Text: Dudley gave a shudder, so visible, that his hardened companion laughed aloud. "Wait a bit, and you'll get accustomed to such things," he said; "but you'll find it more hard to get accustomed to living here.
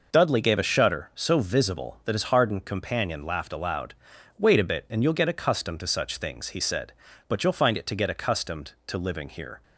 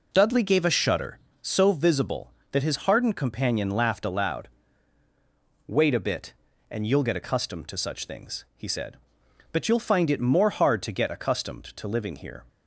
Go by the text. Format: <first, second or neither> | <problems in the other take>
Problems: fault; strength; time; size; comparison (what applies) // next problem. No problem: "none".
second | skips "more hard"; at 7.8 s